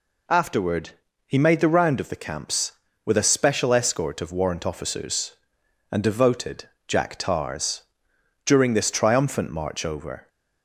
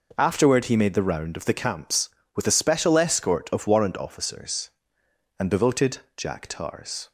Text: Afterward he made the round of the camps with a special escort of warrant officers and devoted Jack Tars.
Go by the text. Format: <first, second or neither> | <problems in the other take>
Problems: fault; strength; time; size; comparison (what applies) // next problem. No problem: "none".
second | pauses between "Afterward" and "he"; slight; at 0.9 s; 0.36 s long // pauses between "devoted" and "Jack"; slight; at 6.6 s; 0.20 s long; slight in the second // goes on to say "During this triumphant march over"; strong; from 8.4 s on; 1.8 s long